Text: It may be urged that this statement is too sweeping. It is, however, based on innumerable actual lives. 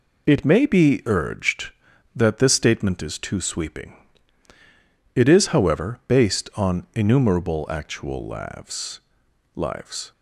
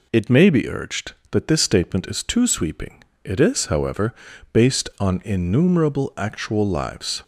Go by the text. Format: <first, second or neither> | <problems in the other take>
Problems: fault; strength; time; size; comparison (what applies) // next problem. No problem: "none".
second | says "lives" twice; at 9.5 s